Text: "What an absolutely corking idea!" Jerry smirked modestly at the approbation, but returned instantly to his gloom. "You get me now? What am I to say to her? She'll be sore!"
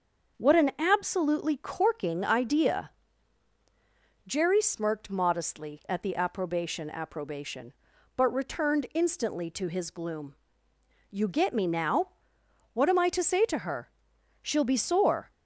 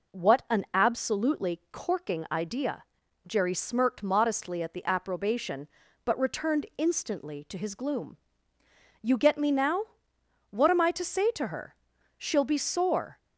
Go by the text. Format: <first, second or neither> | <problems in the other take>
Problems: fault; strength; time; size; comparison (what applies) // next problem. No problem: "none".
second | starts louder than the rest; until 1.4 s; 6.5 dB // says "approbation" twice; at 6.9 s